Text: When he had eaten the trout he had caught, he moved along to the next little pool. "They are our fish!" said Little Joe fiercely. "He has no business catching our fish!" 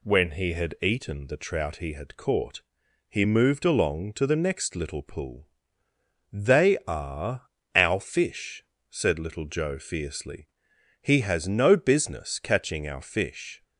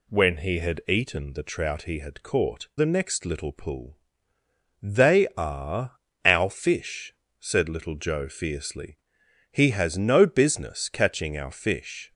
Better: first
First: pauses between "are" and "our"; slight; at 7.4 s; 0.26 s long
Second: skips "he moved along to"; at 2.7 s // pauses between "are" and "our"; slight; at 5.9 s; 0.26 s long

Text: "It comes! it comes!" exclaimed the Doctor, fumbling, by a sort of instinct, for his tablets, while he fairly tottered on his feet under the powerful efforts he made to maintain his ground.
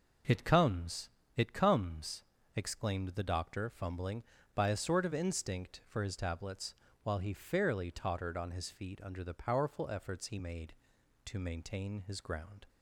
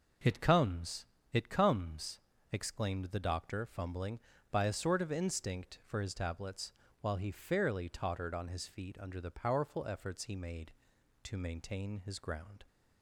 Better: neither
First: none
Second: none

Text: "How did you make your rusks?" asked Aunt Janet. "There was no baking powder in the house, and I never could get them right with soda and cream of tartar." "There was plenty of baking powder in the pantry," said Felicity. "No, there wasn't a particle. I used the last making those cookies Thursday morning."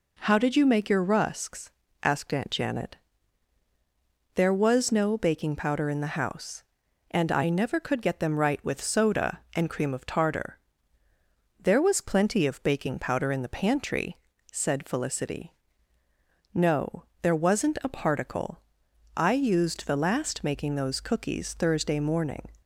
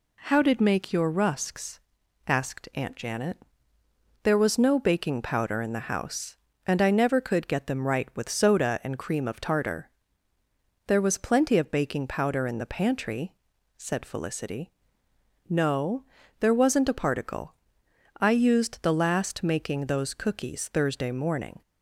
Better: first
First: none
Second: skips "you"; at 0.6 s

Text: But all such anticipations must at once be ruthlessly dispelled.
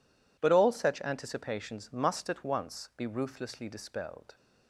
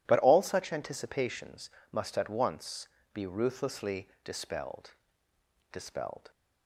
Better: first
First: none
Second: pauses between "anticipations" and "must"; slight; at 1.6 s; 0.22 s long // pauses between "once" and "be"; slight; at 2.8 s; 0.26 s long // says "dispelled" twice; at 5.7 s

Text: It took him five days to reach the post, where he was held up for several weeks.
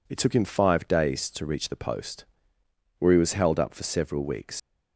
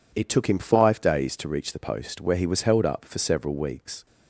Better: second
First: leaves "weeks" unfinished; at 4.5 s; 115 ms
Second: none

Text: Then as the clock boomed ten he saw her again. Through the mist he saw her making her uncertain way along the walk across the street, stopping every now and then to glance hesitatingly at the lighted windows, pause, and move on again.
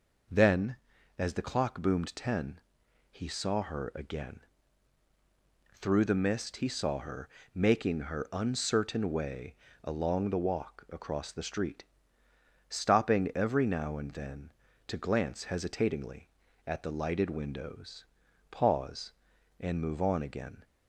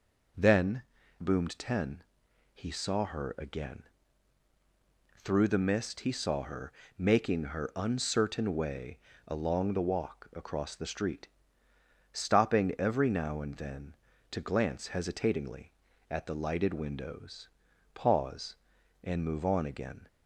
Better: first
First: pauses between "ten" and "he"; noticeable; at 2.5 s; 0.50 s long // pauses between "her" and "making"; slight; at 7.2 s; 0.24 s long // pauses between "way" and "along"; slight; at 9.5 s; 0.28 s long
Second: skips "as the clock"; at 1.0 s // pauses between "ten" and "he"; noticeable; at 2.0 s; 0.50 s long // pauses between "her" and "making"; slight; at 6.7 s; 0.24 s long // pauses between "way" and "along"; slight; at 8.9 s; 0.28 s long

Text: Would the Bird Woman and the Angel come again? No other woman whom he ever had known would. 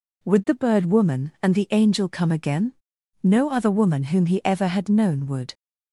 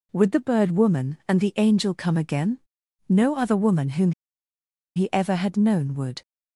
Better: first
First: none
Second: pauses between "whom" and "he"; noticeable; at 4.1 s; 0.82 s long

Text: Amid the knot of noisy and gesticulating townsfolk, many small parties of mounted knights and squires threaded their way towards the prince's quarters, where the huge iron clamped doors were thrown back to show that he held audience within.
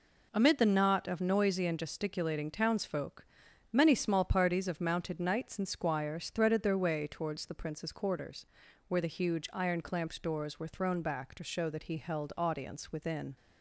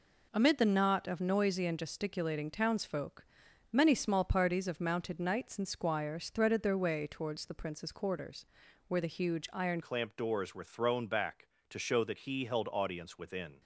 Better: first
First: none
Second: changes voice at "clamped"; from 9.8 s on; 3.8 s long

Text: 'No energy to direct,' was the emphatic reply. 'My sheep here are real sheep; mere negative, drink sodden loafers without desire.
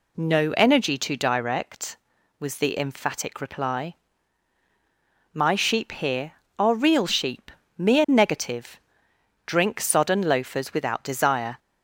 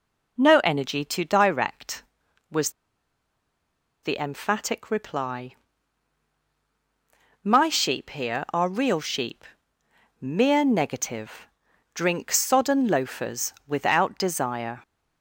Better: first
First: none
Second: pauses between "was" and "the"; strong; at 2.6 s; 1.3 s long // pauses between "loafers" and "without"; slight; at 13.5 s; 0.16 s long

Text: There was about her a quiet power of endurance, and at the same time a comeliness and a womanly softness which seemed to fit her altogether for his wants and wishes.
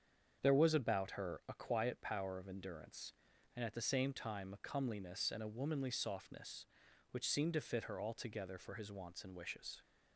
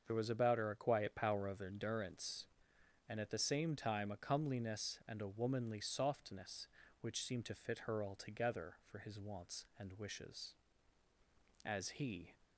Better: first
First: starts louder than the rest; strong; until 1.4 s; 7.5 dB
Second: starts louder than the rest; until 1.0 s; 6.5 dB // goes on to say "As he"; noticeable; from 11.6 s on; 0.68 s long

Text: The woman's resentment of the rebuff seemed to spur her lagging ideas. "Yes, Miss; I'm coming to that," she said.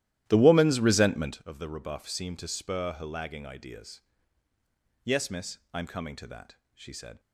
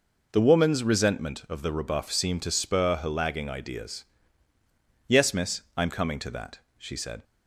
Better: second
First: starts louder than the rest; strong; until 1.5 s; 13.5 dB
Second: none

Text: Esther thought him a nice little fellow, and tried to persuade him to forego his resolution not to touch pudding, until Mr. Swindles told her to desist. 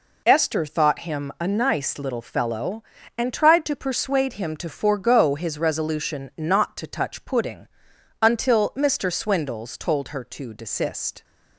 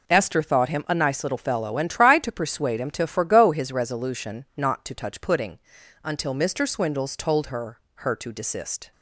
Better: first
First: none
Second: says "her" twice; at 7.9 s

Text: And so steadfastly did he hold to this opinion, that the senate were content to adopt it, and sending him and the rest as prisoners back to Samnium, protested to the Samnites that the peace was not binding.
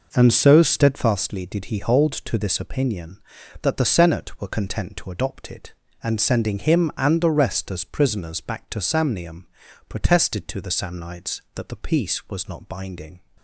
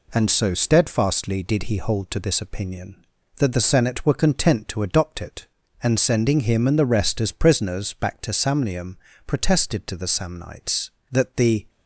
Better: first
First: none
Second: stops before "peace was not binding"; at 11.6 s

